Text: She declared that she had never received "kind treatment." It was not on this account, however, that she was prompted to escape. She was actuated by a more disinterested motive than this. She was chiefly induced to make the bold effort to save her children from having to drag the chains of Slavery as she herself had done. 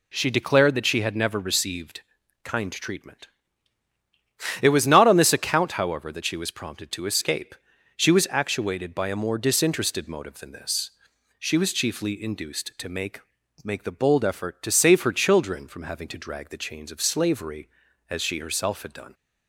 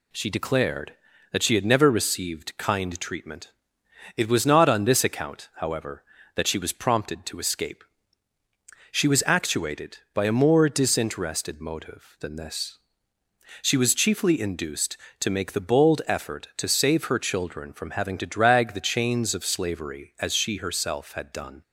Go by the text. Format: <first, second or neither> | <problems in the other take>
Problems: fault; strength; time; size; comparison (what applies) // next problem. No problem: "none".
second | pauses between "received" and "kind"; at 2.0 s; 0.42 s long // says "make" twice; at 13.6 s